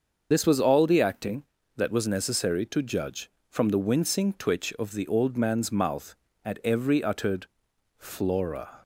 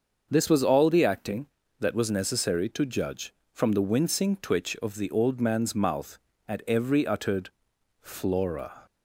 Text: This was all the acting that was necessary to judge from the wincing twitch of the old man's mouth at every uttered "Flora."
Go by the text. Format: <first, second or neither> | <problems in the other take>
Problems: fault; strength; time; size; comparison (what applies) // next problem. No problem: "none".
second | loses the start of "This"; at 0.3 s; 35 ms // starts louder than the rest; until 1.3 s; 6.5 dB; also in the second // pauses between "uttered" and "Flora"; noticeable; at 7.4 s; 0.50 s long; noticeable in the second